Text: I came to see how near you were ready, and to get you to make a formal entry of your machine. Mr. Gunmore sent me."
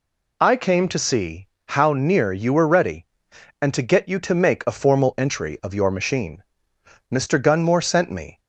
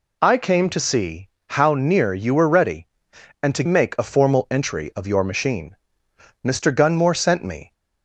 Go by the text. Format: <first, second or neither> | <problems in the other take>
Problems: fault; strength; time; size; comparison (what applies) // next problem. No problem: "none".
first | pauses between "see" and "how"; slight; at 1.2 s; 0.22 s long; slight in the first // skips "get you to"; at 3.6 s